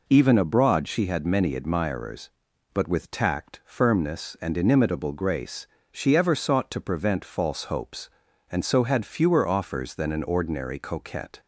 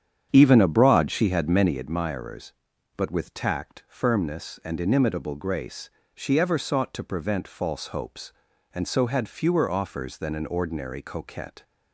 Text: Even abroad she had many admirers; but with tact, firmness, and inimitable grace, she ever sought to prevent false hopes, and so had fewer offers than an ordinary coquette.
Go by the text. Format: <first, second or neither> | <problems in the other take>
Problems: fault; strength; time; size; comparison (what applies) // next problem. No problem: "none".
first | starts louder than the rest; strong; until 1.8 s; 8.5 dB